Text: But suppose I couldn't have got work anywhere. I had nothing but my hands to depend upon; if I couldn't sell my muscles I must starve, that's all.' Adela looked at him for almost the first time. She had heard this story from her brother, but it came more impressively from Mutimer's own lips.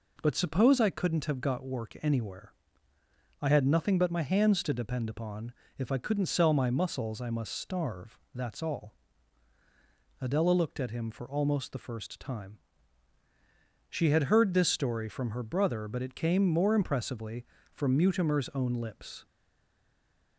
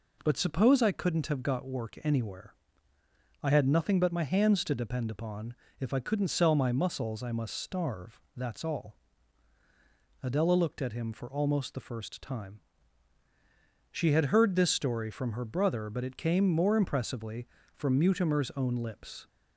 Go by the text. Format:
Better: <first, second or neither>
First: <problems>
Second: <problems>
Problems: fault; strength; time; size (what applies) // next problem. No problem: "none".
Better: second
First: stays silent after the last word; from 19.2 s on; 1.1 s long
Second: none